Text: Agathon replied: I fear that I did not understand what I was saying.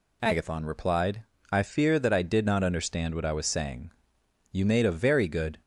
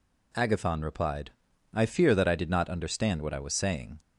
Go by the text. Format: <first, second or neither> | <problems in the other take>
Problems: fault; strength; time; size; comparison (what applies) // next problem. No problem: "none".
second | goes on to say "You made a very good"; noticeable; from 4.5 s on; 1.0 s long